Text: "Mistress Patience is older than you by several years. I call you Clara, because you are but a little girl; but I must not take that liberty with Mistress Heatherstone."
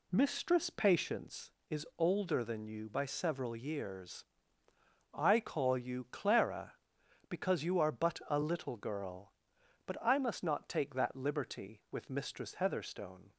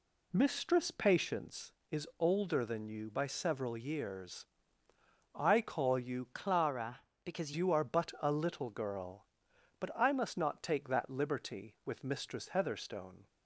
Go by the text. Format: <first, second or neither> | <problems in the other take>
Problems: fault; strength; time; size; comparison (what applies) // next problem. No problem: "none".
first | changes voice from "Clara" to "because"; from 6.3 to 7.5 s; 1.2 s long